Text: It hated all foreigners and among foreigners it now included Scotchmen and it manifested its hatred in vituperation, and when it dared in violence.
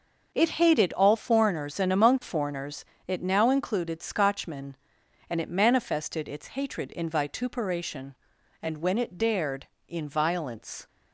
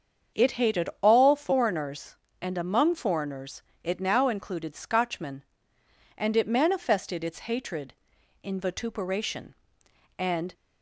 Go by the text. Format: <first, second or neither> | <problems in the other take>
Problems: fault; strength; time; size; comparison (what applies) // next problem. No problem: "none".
first | starts louder than the rest; until 1.4 s; 7 dB; noticeable in the first // pauses between "foreigners" and "it"; slight; at 3.6 s; 0.22 s long; slight in the first // stops before "when it dared in violence"; at 10.5 s